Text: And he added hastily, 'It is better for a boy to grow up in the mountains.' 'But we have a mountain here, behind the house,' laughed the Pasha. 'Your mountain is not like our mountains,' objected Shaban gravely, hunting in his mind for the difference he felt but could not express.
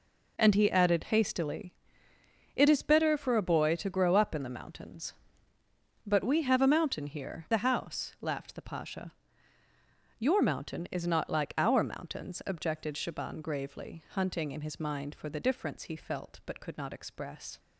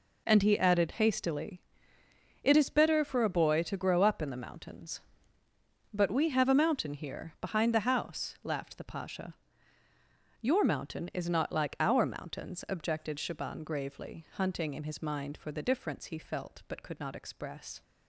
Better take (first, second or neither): second